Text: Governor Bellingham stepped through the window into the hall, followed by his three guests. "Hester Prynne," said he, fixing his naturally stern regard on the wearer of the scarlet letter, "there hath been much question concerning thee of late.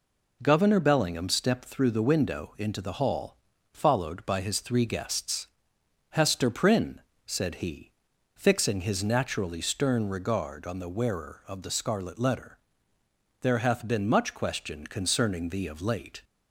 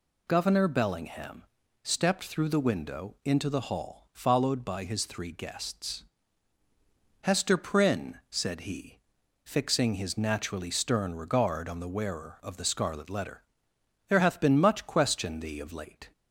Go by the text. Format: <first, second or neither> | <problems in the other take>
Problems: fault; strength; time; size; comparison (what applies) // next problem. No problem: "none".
first | pauses between "Bellingham" and "stepped"; at 1.4 s; 0.40 s long // skips "concerning"; at 15.3 s